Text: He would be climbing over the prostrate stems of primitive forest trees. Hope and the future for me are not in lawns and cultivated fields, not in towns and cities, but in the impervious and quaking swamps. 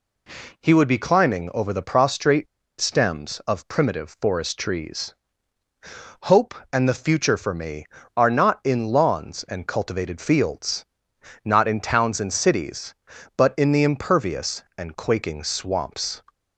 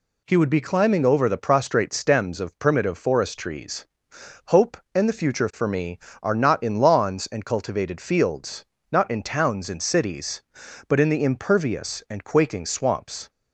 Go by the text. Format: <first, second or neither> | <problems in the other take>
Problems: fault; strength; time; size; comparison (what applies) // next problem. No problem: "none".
second | pauses between "prostrate" and "stems"; slight; at 2.4 s; 0.35 s long